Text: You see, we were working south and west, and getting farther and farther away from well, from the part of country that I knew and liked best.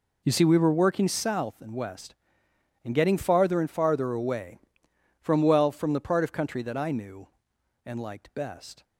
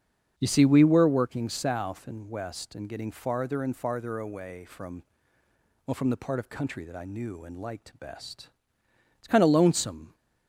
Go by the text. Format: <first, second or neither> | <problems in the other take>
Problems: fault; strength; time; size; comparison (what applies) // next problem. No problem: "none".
first | starts louder than the rest; until 1.3 s; 7 dB // pauses between "from" and "well"; noticeable; at 5.0 s; 0.84 s long // goes on to say "It's kind of lonesome"; noticeable; from 9.2 s on; 0.92 s long